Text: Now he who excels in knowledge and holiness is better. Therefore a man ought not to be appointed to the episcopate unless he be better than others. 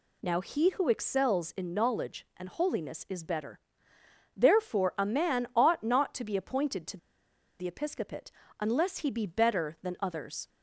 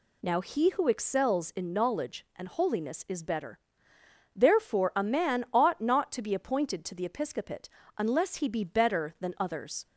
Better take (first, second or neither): second